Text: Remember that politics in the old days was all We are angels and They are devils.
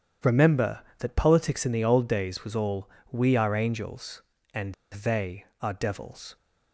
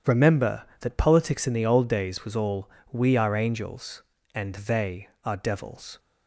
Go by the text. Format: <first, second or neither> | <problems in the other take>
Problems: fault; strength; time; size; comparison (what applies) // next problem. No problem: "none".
second | starts louder than the rest; strong; until 1.4 s; 9 dB; strong in the second // pauses between "all" and "We"; slight; at 2.8 s; 0.24 s long; slight in the second // pauses between "and" and "They"; slight; at 4.7 s; 0.17 s long